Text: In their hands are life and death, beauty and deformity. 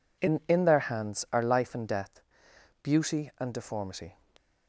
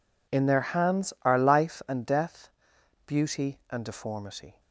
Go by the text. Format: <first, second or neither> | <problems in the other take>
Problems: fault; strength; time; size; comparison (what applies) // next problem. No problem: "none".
second | says "In" twice; at 0.4 s